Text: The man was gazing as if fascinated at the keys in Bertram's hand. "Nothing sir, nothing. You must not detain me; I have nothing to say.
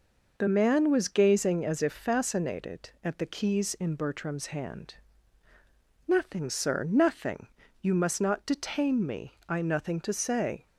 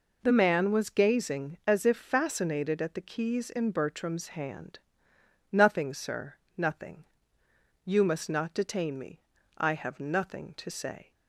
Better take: second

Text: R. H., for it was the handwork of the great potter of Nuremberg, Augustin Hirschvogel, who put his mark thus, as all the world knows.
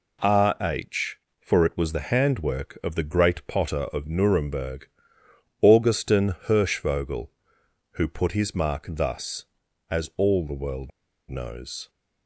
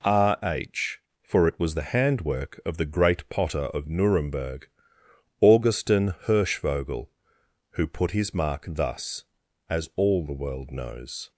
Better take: second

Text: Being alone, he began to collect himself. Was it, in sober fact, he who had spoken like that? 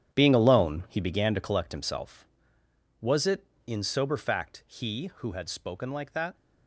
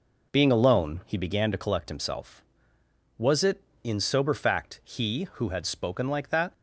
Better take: second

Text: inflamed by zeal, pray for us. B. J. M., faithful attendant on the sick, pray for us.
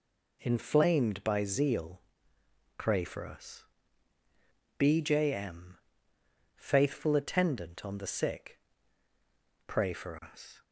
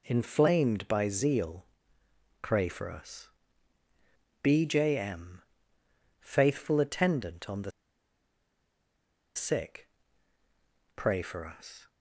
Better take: first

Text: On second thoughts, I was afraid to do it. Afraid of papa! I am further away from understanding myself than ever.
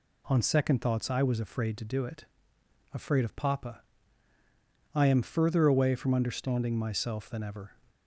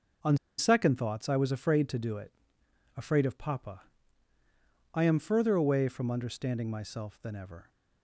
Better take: first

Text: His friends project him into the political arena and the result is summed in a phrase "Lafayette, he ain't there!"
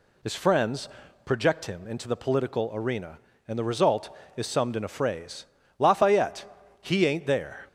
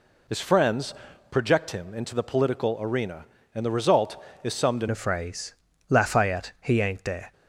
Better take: first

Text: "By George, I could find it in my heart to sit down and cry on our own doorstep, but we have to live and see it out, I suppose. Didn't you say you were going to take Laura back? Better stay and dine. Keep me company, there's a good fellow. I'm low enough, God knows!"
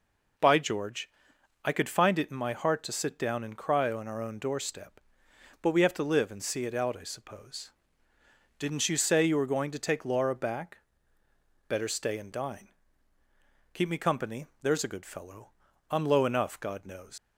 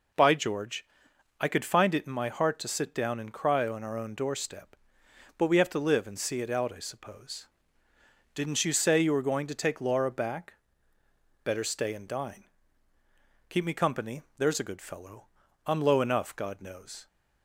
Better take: second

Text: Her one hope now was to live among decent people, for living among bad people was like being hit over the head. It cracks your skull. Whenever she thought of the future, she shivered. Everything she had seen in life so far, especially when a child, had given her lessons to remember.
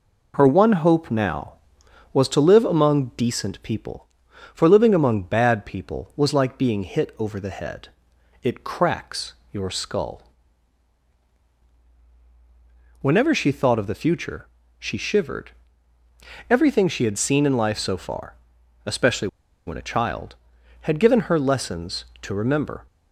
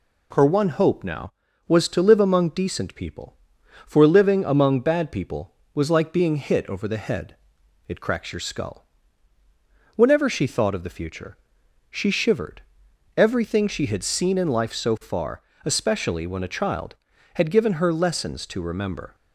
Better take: second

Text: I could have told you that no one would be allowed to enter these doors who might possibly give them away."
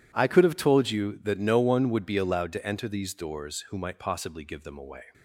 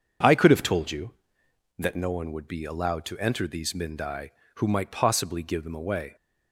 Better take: first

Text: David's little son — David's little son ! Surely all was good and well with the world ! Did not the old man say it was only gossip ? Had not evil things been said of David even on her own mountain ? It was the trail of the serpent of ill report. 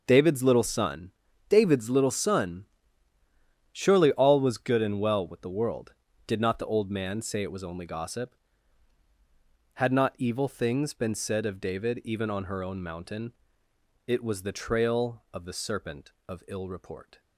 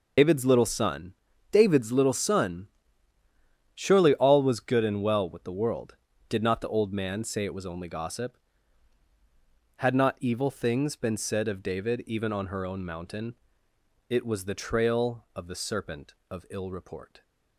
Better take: first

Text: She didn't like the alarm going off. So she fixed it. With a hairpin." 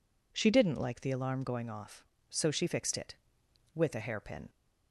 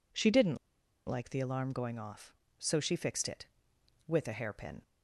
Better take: first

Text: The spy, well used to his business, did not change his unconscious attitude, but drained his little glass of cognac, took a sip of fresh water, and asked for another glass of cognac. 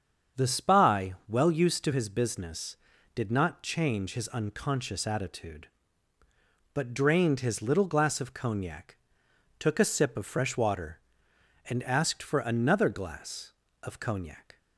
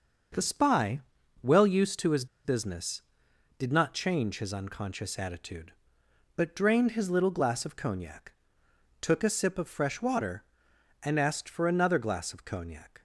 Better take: first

